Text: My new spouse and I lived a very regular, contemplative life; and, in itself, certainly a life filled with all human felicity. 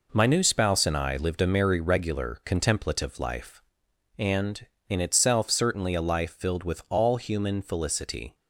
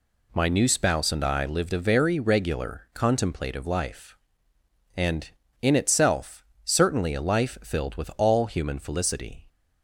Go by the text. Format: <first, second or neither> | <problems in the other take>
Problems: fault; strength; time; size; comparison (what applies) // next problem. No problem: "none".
second | says "merry" for "very"; at 1.4 s